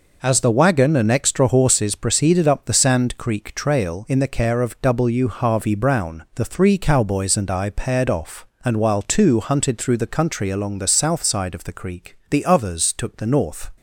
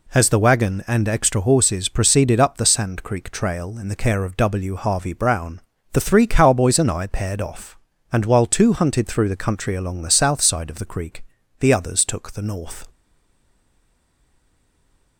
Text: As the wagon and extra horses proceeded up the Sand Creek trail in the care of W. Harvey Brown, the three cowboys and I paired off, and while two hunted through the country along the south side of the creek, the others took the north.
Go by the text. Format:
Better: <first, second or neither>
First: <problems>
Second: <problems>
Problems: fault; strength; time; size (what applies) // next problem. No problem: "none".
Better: first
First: none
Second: stays silent after the last word; from 12.9 s on; 2.2 s long